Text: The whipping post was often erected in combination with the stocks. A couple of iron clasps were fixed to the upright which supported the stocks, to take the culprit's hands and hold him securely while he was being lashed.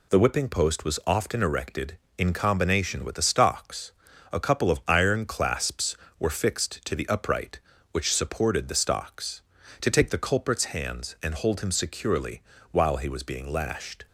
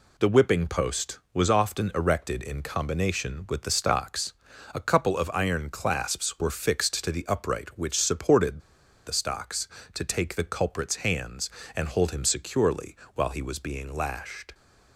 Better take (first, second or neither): first